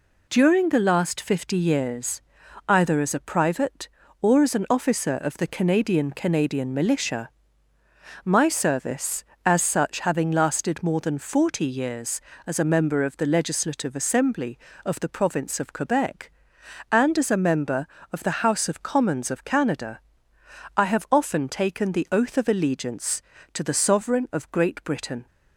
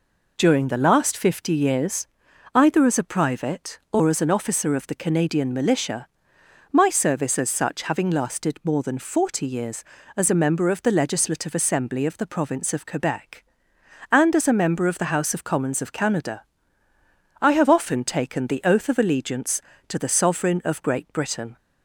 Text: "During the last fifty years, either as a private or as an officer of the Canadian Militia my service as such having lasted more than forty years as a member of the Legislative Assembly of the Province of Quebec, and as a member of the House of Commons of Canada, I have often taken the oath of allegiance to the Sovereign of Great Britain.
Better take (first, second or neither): second